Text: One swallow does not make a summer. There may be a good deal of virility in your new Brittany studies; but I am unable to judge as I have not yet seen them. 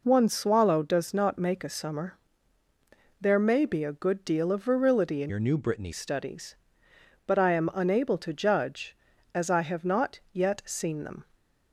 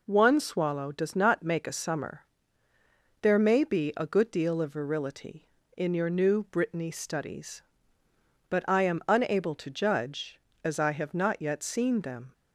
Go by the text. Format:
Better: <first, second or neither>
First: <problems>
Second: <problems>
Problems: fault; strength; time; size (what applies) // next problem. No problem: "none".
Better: second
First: changes voice from "your" to "Brittany"; from 5.2 to 5.9 s; 0.7 s long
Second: none